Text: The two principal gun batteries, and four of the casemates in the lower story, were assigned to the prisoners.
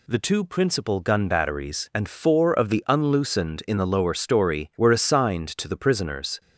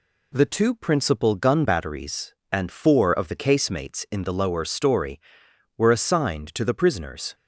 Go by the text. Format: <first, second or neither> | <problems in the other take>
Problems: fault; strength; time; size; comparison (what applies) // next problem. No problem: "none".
second | says "unloosened" for "casemates"; at 2.8 s